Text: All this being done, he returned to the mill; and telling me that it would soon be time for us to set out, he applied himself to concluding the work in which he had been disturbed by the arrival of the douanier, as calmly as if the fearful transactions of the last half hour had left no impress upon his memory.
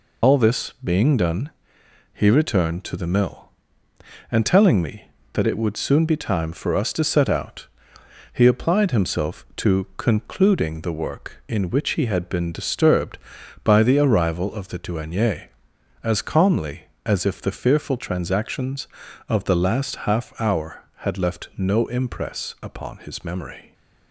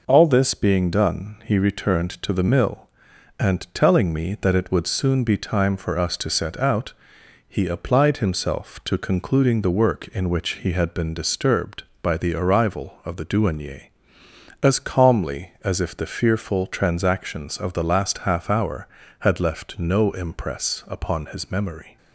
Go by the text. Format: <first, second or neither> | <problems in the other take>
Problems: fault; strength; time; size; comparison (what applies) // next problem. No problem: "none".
second | loses the start of "All"; at 0.2 s; 100 ms